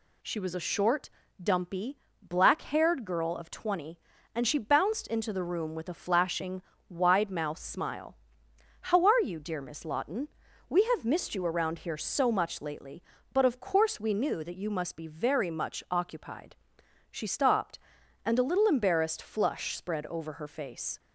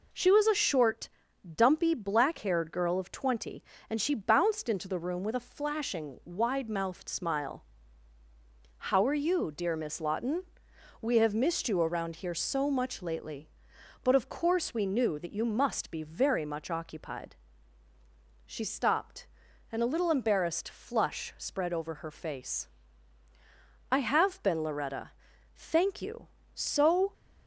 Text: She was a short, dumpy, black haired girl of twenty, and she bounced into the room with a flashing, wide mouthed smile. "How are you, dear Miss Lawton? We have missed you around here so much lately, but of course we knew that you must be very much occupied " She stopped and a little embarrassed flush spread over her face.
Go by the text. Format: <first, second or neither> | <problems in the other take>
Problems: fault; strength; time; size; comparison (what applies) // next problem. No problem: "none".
first | goes on to say "I have been Loretta Thank you so"; strong; from 23.8 s on; 3.2 s long